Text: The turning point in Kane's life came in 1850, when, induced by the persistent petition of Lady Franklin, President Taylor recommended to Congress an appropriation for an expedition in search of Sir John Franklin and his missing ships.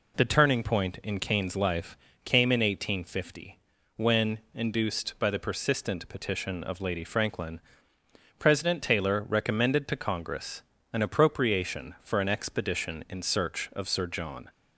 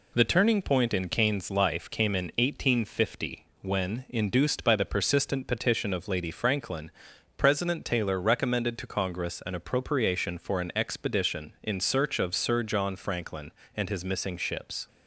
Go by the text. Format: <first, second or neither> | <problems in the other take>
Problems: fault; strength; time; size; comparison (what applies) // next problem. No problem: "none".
second | pauses between "life" and "came"; slight; at 1.9 s; 0.26 s long // pauses between "Congress" and "an"; slight; at 10.6 s; 0.32 s long // stops before "Franklin and his missing ships"; at 14.4 s